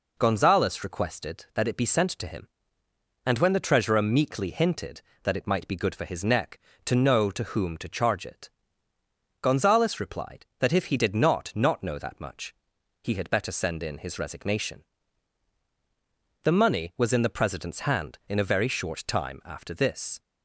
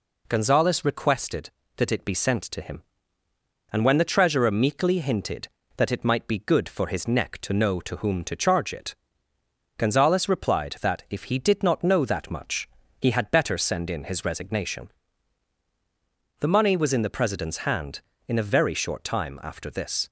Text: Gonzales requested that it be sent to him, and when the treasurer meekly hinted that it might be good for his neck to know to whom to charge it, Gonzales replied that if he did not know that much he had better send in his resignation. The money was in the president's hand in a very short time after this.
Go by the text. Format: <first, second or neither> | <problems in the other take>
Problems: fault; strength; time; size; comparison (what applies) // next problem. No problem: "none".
second | says "not" twice; at 11.5 s // pauses between "much" and "he"; noticeable; at 12.5 s; 0.48 s long; slight in the second